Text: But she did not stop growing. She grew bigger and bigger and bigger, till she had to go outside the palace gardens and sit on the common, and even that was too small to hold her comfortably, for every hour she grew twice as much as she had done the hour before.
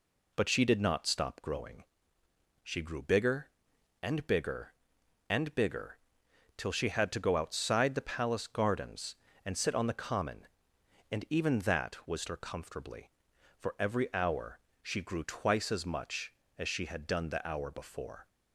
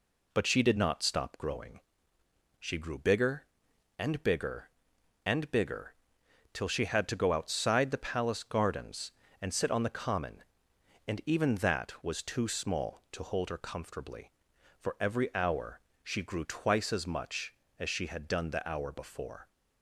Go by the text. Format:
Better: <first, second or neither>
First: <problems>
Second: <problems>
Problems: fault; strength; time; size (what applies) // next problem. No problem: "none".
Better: second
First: skips "too small to hold"; at 12.2 s // pauses between "hour" and "she"; slight; at 14.5 s; 0.24 s long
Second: pauses between "hour" and "she"; slight; at 15.7 s; 0.24 s long